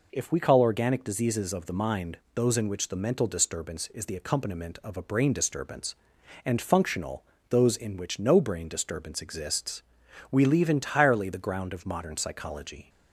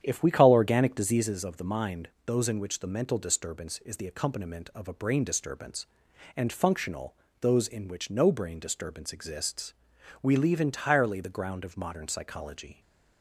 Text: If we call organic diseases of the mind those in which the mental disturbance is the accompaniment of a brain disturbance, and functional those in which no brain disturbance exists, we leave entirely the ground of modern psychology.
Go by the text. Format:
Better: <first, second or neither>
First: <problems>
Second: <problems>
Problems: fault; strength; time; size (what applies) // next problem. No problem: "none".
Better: first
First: pauses between "mind" and "those"; slight; at 2.1 s; 0.18 s long // pauses between "functional" and "those"; slight; at 7.2 s; 0.26 s long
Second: starts louder than the rest; strong; until 1.3 s; 9 dB // pauses between "mind" and "those"; slight; at 2.0 s; 0.18 s long // pauses between "functional" and "those"; slight; at 7.1 s; 0.26 s long